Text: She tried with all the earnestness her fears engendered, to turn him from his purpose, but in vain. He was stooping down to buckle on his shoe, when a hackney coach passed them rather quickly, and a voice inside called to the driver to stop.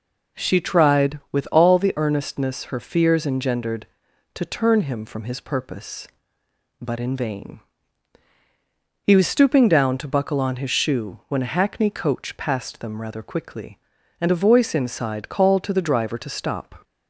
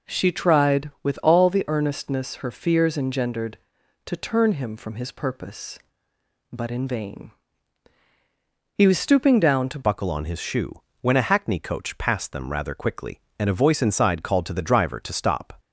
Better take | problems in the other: first | changes voice at "buckle"; from 9.8 s on; 5.7 s long

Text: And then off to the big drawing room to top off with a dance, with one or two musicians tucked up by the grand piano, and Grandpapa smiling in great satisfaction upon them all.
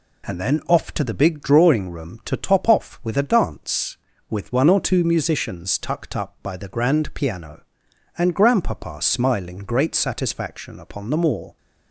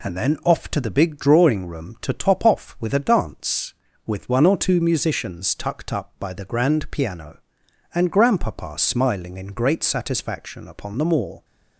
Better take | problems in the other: second | skips "in"; at 9.5 s

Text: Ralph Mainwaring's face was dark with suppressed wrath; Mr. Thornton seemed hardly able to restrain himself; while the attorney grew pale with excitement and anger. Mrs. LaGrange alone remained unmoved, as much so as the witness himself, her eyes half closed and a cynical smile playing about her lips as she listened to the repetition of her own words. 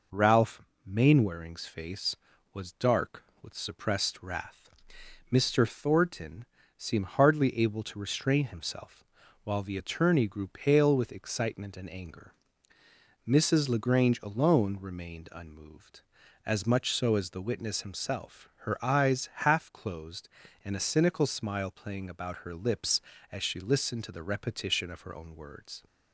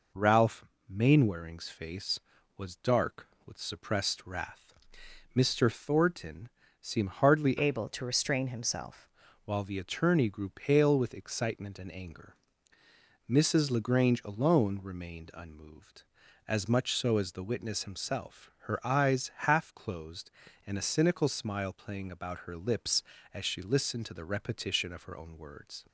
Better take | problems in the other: first | pauses between "Ralph" and "Mainwaring's"; slight; at 0.6 s; 0.24 s long; slight in the first // pauses between "Thornton" and "seemed"; slight; at 6.4 s; 0.30 s long; slight in the first // changes voice from "able" to "himself"; from 7.5 to 9.0 s; 1.5 s long // pauses between "eyes" and "half"; slight; at 19.3 s; 0.16 s long; slight in the first

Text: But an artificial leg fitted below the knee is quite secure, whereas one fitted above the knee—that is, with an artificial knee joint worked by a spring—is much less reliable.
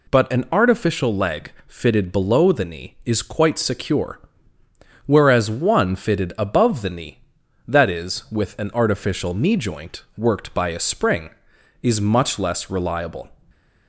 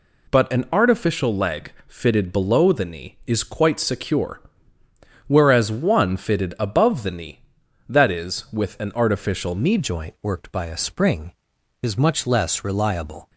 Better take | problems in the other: first | changes voice at "joint"; from 9.7 s on; 3.5 s long

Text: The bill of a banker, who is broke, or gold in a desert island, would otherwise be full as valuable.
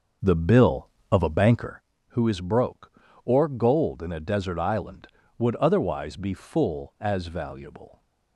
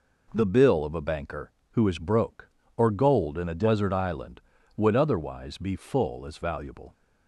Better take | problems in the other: second | starts louder than the rest; noticeable; until 1.9 s; 6 dB

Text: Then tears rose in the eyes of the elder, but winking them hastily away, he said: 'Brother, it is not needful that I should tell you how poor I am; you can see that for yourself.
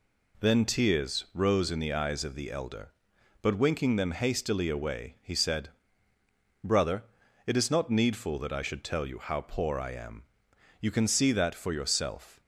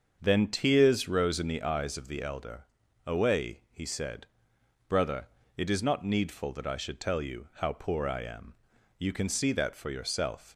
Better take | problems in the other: first | starts louder than the rest; until 1.2 s; 7 dB // skips "but winking them hastily"; at 2.8 s

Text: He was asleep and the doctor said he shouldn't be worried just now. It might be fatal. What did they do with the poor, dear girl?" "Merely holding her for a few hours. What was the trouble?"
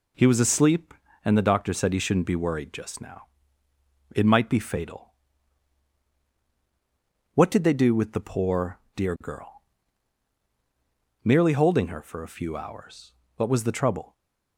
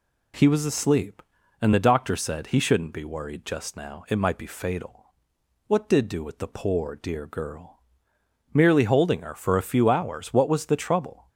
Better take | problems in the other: first | skips "they"; at 6.0 s

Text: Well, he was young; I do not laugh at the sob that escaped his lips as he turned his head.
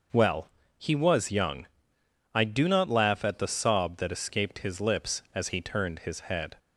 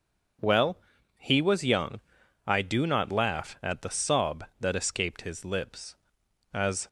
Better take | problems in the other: first | stops before "he turned his head"; at 6.8 s

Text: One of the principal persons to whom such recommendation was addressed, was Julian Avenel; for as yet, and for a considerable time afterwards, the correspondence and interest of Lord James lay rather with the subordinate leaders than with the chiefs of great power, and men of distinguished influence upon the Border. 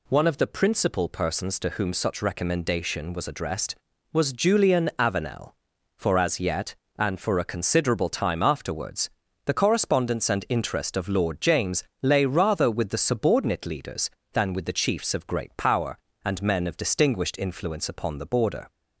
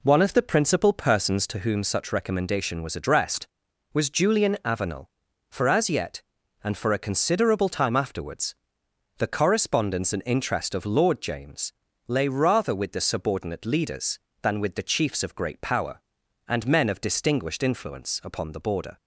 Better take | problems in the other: first | starts louder than the rest; slight; until 1.7 s; 3 dB // pauses between "James" and "lay"; slight; at 11.7 s; 0.34 s long; slight in the first

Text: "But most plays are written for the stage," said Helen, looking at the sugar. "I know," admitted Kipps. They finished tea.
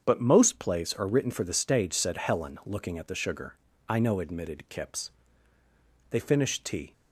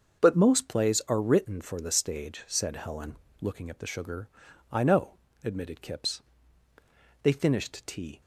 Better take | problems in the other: neither | starts louder than the rest; the same in both

